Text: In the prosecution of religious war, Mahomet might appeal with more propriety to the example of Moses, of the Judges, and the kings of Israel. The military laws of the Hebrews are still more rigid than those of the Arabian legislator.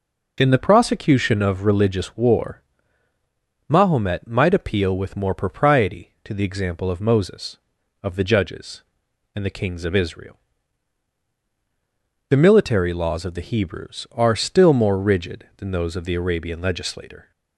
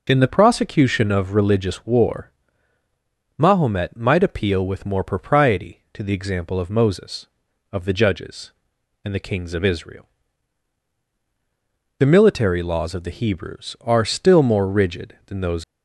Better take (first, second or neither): first